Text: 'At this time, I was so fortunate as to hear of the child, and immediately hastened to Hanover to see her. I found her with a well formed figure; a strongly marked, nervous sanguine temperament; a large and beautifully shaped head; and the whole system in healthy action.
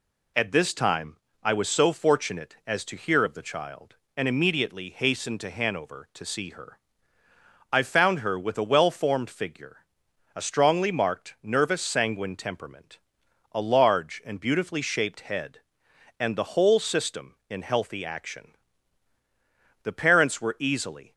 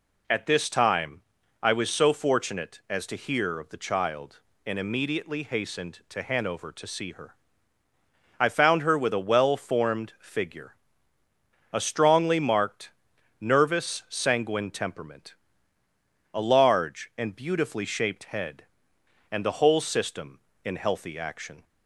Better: second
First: goes on to say "The parents were easily"; noticeable; from 19.8 s on; 1.3 s long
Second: none

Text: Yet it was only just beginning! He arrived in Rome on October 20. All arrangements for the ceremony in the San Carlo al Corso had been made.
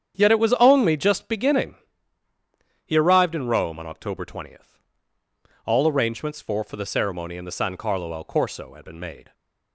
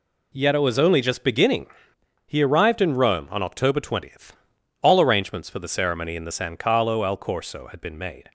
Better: second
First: starts louder than the rest; strong; until 1.1 s; 9 dB // says "for" twice; at 6.6 s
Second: none

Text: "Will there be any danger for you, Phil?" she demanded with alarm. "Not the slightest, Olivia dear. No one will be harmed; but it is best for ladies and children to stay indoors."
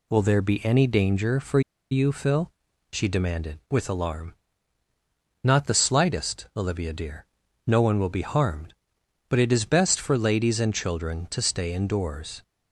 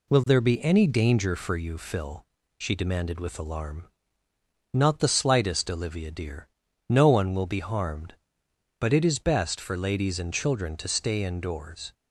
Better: second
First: pauses between "for" and "you"; slight; at 1.5 s; 0.31 s long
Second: none

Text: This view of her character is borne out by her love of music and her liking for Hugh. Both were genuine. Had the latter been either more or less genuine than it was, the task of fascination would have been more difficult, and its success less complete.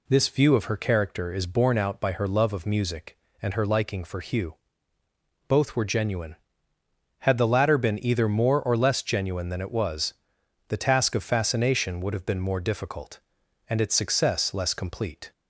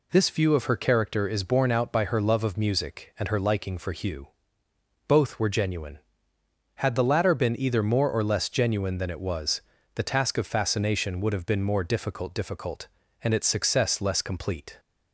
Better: first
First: none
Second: says "difficult" twice; at 12.3 s

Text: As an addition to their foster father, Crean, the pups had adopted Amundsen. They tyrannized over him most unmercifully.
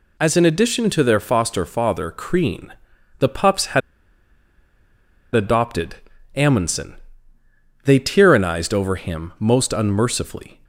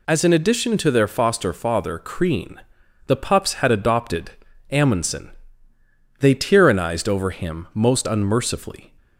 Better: second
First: pauses between "had" and "adopted"; strong; at 3.8 s; 1.5 s long // pauses between "adopted" and "Amundsen"; at 5.9 s; 0.40 s long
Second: pauses between "adopted" and "Amundsen"; at 4.3 s; 0.40 s long

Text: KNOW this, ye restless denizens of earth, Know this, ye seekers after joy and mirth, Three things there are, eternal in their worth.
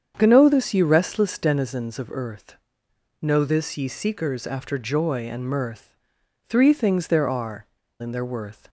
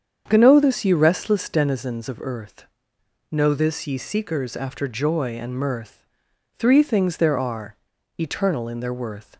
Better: second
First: starts louder than the rest; strong; until 1.1 s; 7.5 dB // skips "eternal"; at 7.8 s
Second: starts louder than the rest; strong; until 1.2 s; 7.5 dB

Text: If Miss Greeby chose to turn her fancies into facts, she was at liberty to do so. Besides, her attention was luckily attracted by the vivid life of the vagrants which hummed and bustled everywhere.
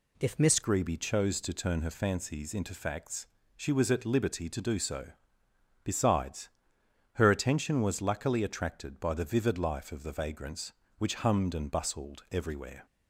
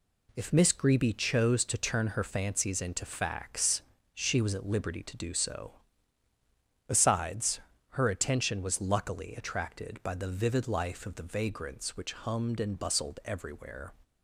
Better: second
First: changes voice at "Greeby"; from 0.6 s on; 12.2 s long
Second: none

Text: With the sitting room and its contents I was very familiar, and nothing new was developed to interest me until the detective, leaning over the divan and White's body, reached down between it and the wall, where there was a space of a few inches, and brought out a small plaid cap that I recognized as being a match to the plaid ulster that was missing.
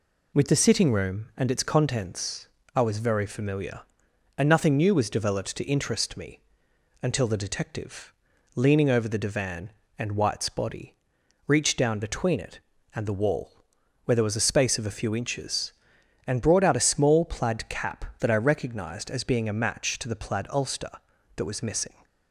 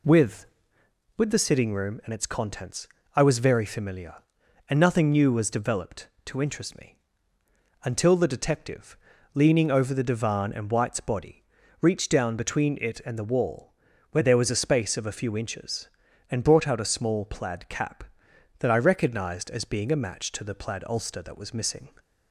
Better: first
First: pauses between "contents" and "I"; slight; at 2.4 s; 0.28 s long // pauses between "me" and "until"; noticeable; at 6.4 s; 0.60 s long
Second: says "With" twice; at 1.1 s // pauses between "contents" and "I"; slight; at 2.8 s; 0.28 s long // pauses between "me" and "until"; noticeable; at 6.9 s; 0.86 s long

